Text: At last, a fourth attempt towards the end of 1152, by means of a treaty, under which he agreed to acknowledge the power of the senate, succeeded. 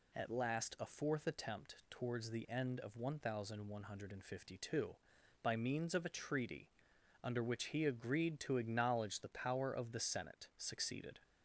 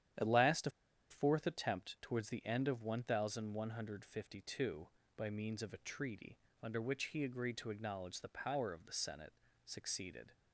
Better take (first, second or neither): first